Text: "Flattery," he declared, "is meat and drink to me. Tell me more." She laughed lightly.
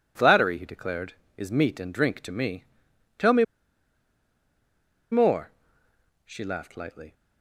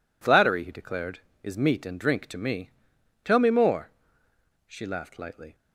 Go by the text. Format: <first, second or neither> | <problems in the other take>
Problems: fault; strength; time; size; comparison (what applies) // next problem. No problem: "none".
second | pauses between "me" and "more"; strong; at 3.4 s; 1.6 s long